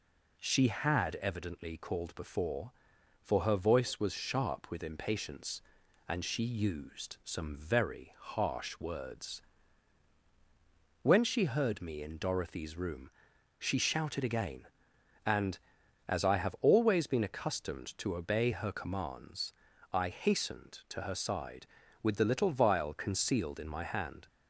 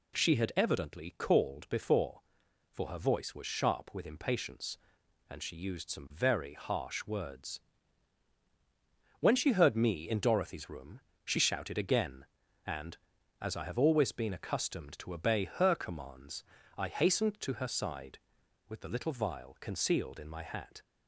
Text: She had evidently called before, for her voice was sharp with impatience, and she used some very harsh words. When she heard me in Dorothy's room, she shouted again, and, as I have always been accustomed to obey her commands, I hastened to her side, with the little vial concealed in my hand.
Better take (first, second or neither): first